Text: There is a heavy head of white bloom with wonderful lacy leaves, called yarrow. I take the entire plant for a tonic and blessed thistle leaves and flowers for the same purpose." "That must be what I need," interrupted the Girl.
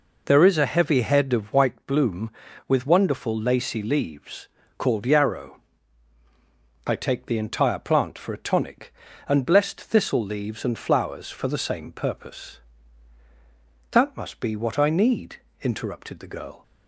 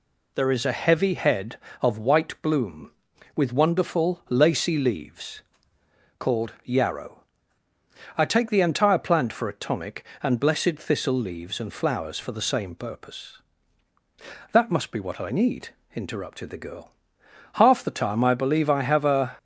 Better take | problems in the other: first | goes on to say "Half the time I believe I have a"; strong; from 17.5 s on; 1.8 s long

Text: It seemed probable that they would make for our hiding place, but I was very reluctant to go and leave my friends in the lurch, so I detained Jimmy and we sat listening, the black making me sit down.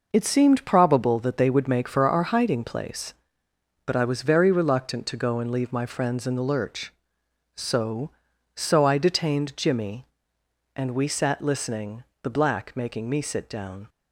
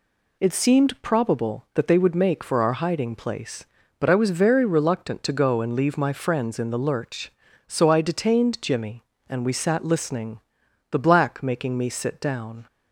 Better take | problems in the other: second | says "so" twice; at 8.5 s

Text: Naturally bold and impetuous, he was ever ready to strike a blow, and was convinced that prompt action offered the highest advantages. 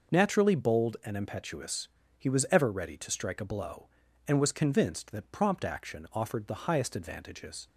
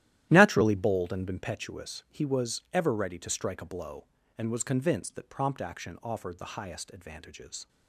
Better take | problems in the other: first | starts louder than the rest; strong; until 1.5 s; 13 dB

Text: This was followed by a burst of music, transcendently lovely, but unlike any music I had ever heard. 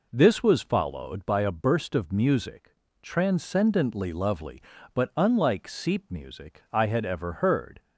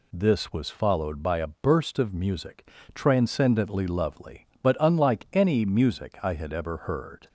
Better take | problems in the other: second | says "seep" for "any"; at 5.6 s

